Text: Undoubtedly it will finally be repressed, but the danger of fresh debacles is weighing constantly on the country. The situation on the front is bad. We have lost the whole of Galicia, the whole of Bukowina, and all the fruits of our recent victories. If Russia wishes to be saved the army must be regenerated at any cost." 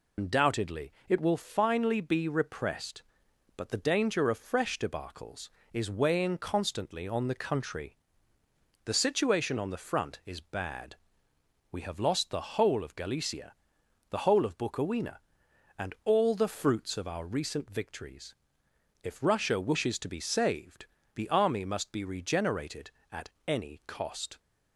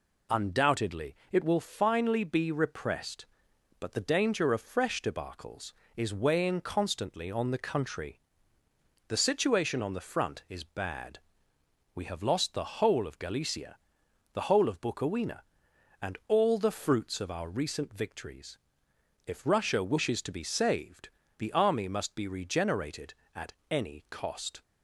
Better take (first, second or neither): second